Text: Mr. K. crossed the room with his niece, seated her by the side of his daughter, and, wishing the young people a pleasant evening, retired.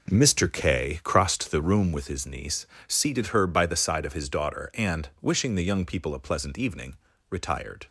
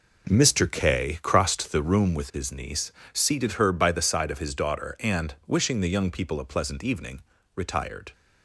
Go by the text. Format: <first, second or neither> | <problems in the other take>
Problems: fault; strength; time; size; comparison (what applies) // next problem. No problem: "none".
neither | none